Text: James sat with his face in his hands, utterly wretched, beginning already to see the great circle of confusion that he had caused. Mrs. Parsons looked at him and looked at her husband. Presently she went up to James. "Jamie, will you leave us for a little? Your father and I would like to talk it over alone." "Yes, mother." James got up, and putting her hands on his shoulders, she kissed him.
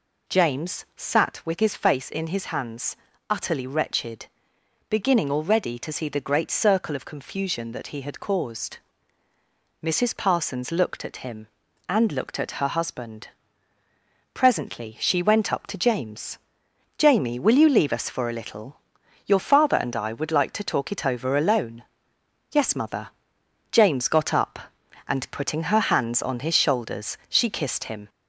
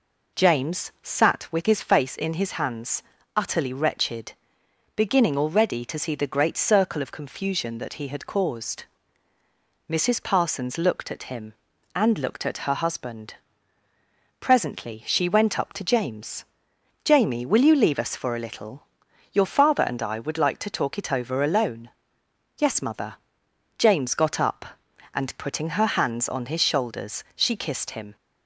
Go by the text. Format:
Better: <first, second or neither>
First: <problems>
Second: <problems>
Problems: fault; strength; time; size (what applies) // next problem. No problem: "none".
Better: second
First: gets louder; slight; throughout; 2.5 dB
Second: none